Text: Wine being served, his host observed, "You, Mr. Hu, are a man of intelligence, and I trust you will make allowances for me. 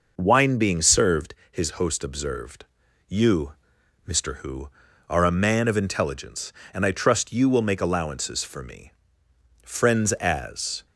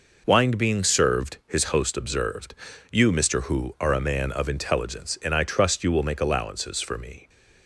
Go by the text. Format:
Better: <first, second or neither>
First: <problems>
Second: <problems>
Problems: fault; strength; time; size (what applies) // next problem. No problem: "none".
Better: second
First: goes on to say "Friends as"; noticeable; from 9.6 s on; 1.2 s long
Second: none